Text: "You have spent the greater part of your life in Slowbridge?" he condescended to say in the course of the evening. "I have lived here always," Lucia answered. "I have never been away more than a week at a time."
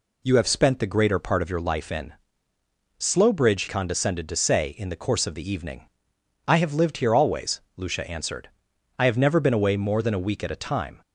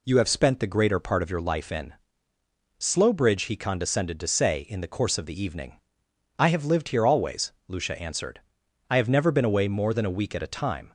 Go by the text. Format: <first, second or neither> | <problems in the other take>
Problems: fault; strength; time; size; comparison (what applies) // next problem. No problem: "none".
second | pauses between "in" and "Slowbridge"; noticeable; at 2.1 s; 0.86 s long; noticeable in the second // skips "he"; at 3.6 s